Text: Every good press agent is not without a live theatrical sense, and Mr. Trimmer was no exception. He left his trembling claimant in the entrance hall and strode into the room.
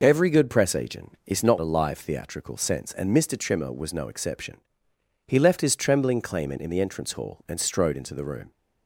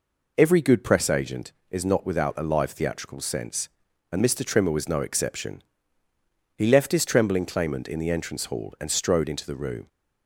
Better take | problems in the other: second | skips "without"; at 1.5 s

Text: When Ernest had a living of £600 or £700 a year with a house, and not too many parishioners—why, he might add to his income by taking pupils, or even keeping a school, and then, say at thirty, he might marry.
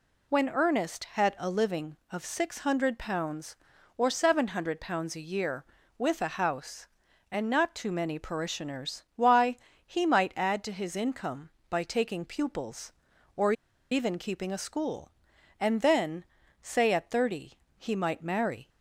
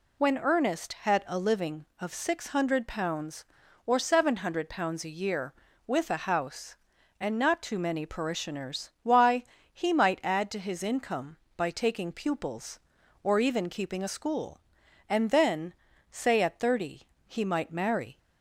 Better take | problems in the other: second | pauses between "or" and "even"; at 13.5 s; 0.38 s long

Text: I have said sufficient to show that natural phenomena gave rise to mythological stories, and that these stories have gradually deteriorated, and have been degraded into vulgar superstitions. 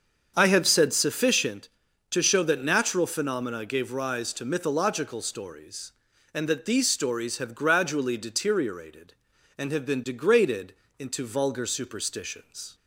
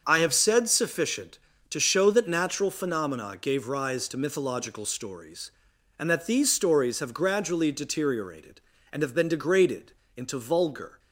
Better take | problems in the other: first | starts louder than the rest; until 1.0 s; 6.5 dB; also in the first // pauses between "degraded" and "into"; slight; at 9.9 s; 0.24 s long; slight in the first // stops before "superstitions"; at 10.9 s

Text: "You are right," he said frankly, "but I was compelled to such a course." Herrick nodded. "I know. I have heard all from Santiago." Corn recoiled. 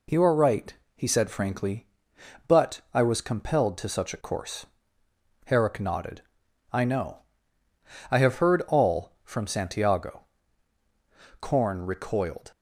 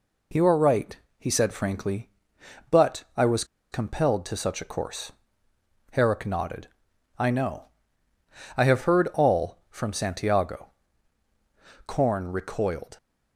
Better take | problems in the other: first | pauses between "was" and "compelled"; slight; at 3.4 s; 0.27 s long

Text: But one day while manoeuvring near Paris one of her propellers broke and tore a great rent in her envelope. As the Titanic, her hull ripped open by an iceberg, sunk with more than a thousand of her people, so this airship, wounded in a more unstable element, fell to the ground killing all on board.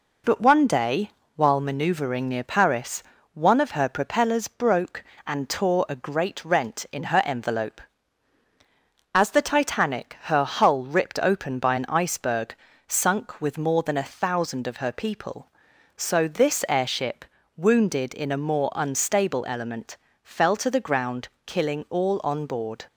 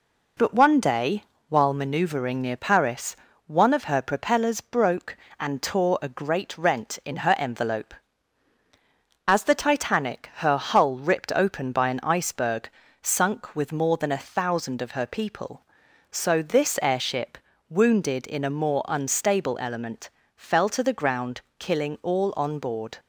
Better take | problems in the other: neither | pauses between "day" and "while"; slight; the same in both // pauses between "Paris" and "one"; slight; the same in both // pauses between "ground" and "killing"; slight; the same in both

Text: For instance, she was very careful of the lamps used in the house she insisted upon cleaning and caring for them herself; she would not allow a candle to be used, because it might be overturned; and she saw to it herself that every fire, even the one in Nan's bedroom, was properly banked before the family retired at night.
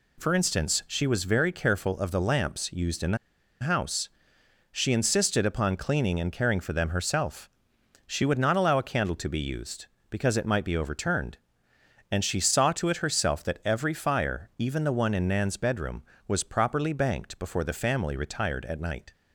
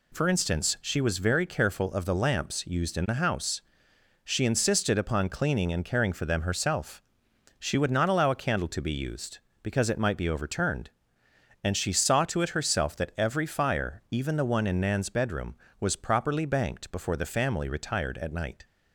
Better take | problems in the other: second | pauses between "the" and "house"; at 3.1 s; 0.44 s long // pauses between "house" and "she"; noticeable; at 4.0 s; 0.66 s long; noticeable in the second

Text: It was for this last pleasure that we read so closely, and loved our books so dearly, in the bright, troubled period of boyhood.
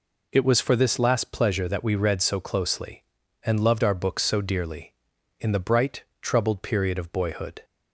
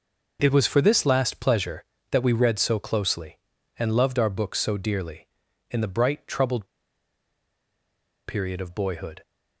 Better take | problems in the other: first | pauses between "troubled" and "period"; strong; at 6.6 s; 1.6 s long

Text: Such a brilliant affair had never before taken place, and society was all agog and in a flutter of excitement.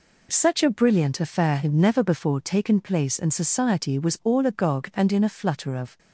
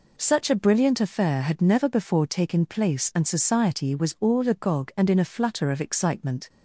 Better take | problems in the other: second | stops before "excitement"; at 5.9 s

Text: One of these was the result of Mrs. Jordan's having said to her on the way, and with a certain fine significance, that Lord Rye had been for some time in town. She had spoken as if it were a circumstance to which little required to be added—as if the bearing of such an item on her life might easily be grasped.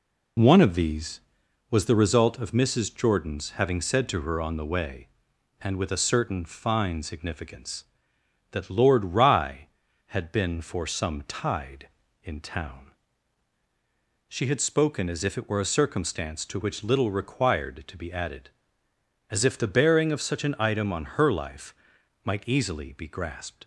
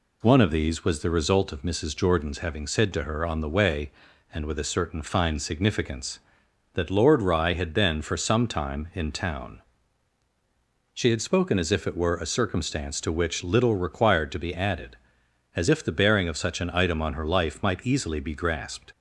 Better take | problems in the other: second | says "tide" for "time"; at 11.2 s // pauses between "life" and "might"; noticeable; at 21.7 s; 0.52 s long

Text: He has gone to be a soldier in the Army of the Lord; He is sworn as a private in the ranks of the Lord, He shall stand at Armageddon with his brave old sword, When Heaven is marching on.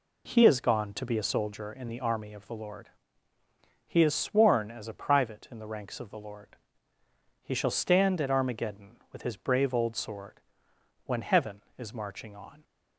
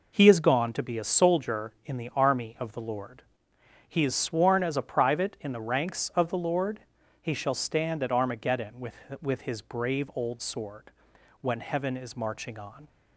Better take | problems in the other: first | says "with" twice; at 9.2 s

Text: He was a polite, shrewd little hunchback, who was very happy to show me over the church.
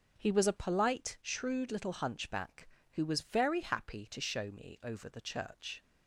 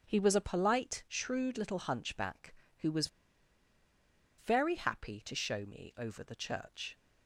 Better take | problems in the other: first | starts louder than the rest; until 1.1 s; 7 dB; also in the first // pauses between "was" and "very"; strong; at 3.0 s; 1.3 s long

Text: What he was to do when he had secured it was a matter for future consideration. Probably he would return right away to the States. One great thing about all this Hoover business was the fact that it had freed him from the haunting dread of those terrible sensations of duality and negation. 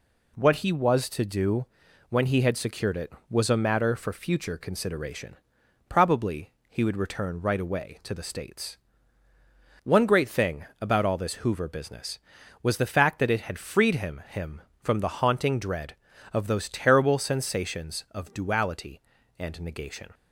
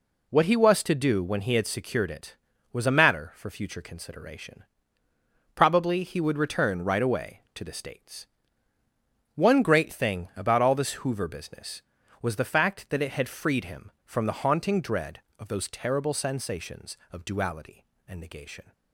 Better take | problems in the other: second | pauses between "do" and "when"; at 1.6 s; 0.44 s long // pauses between "Probably" and "he"; slight; at 6.5 s; 0.18 s long // pauses between "thing" and "about"; slight; at 10.6 s; 0.16 s long // says "him" twice; at 14.2 s

